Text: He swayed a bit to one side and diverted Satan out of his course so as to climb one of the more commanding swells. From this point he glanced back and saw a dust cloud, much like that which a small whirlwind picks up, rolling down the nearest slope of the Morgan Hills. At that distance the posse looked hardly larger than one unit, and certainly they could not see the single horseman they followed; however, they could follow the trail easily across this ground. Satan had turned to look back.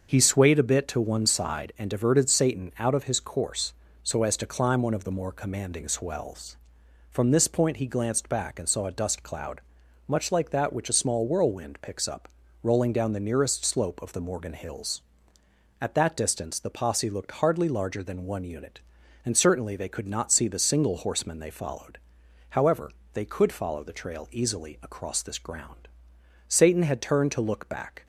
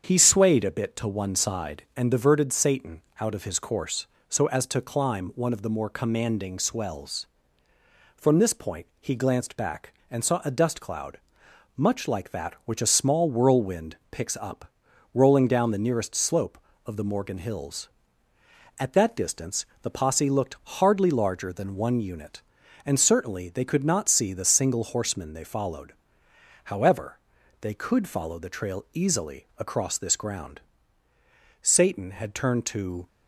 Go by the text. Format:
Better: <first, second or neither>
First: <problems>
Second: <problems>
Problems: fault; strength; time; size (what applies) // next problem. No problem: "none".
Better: first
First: starts louder than the rest; until 1.1 s; 6.5 dB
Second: starts louder than the rest; strong; until 1.0 s; 7.5 dB // pauses between "Satan" and "out"; slight; at 3.0 s; 0.18 s long // pauses between "point" and "he"; slight; at 8.8 s; 0.16 s long // pauses between "distance" and "the"; slight; at 19.6 s; 0.16 s long // stops before "look back"; at 33.0 s